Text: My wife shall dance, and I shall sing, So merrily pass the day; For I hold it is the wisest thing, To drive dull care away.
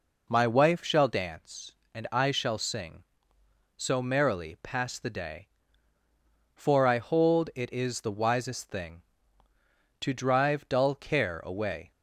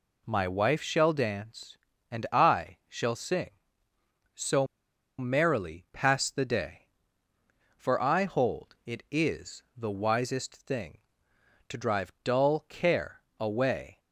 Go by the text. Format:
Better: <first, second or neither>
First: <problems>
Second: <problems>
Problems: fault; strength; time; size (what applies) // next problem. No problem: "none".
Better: first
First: none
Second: pauses between "So" and "merrily"; noticeable; at 4.6 s; 0.52 s long // pauses between "is" and "the"; slight; at 9.6 s; 0.16 s long // pauses between "care" and "away"; slight; at 13.2 s; 0.18 s long